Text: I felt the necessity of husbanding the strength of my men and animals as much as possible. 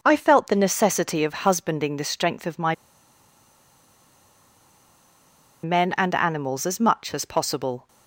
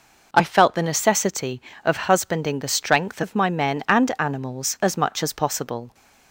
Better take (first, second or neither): second